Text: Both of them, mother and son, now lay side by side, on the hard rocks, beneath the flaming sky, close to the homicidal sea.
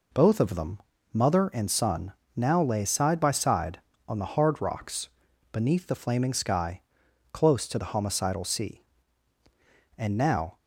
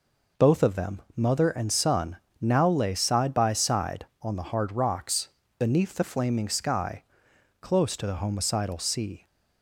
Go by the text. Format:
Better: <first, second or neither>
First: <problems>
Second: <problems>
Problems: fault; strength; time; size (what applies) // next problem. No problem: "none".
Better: second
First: goes on to say "And now"; from 9.9 s on; 0.60 s long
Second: none